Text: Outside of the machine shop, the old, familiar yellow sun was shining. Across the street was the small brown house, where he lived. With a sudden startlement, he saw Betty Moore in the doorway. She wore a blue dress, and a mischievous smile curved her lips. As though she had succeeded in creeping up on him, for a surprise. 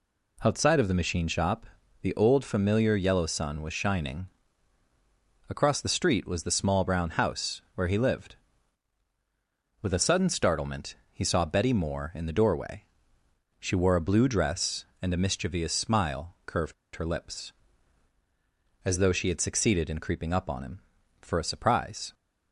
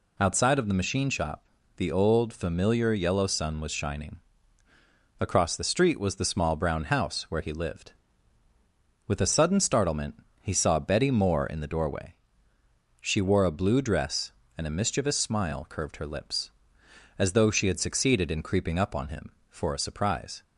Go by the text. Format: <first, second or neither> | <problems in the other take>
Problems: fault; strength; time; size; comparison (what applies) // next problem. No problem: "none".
second | pauses between "curved" and "her"; slight; at 16.7 s; 0.21 s long